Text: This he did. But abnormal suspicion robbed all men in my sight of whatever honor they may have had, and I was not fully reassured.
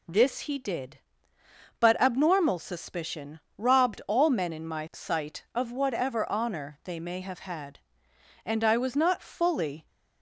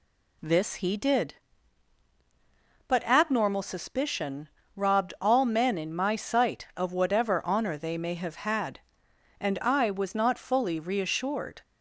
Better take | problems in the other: second | pauses between "suspicion" and "robbed"; slight; at 3.3 s; 0.18 s long; slight in the second // stops before "reassured"; at 9.8 s

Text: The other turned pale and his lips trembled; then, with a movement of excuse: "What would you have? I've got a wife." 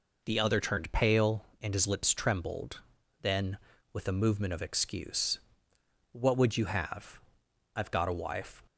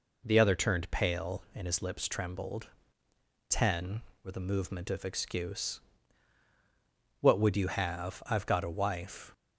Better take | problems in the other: first | says "ten" for "then"; at 3.4 s

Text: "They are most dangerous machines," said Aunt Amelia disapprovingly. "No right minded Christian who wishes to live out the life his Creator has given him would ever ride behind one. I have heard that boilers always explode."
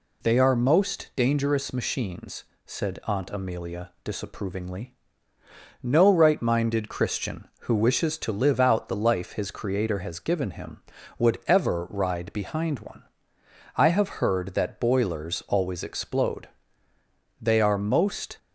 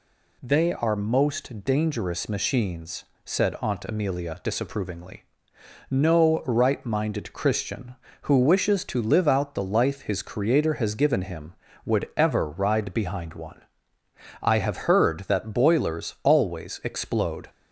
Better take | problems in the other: second | goes on to say "They are most"; noticeable; from 17.3 s on; 0.98 s long

